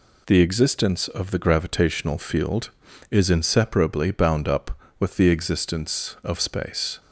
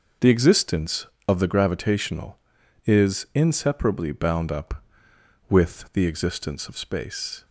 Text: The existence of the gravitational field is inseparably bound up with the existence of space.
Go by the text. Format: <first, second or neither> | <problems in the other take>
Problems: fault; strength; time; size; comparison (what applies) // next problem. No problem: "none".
first | skips "field"; at 2.6 s